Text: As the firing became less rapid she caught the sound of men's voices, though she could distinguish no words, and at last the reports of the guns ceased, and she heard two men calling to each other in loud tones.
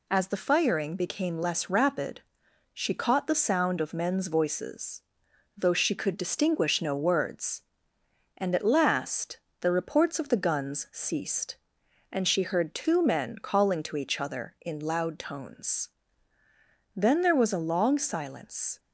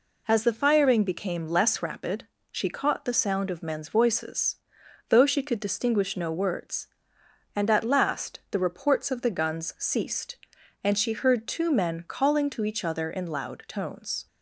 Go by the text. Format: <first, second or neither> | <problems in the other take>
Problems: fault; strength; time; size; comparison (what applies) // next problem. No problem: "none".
second | pauses between "rapid" and "she"; noticeable; at 2.2 s; 0.52 s long; slight in the second // pauses between "last" and "the"; slight; at 9.3 s; 0.24 s long // goes on to say "Then there was a long silence"; strong; from 16.9 s on; 1.8 s long